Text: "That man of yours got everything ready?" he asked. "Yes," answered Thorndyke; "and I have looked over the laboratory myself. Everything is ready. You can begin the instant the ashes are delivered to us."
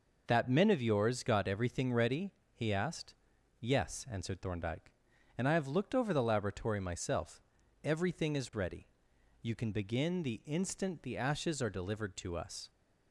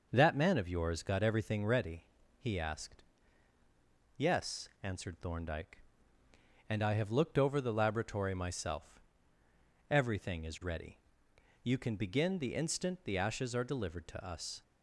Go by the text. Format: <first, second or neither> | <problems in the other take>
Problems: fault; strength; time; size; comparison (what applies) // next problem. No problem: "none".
second | says "men" for "man"; at 0.4 s